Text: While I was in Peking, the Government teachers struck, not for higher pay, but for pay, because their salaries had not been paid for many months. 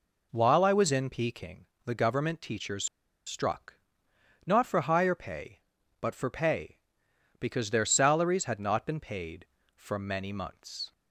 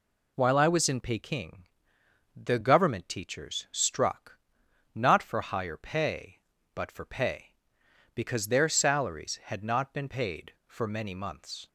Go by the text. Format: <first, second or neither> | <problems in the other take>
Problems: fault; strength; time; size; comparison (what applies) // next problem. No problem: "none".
second | pauses between "teachers" and "struck"; at 2.8 s; 0.41 s long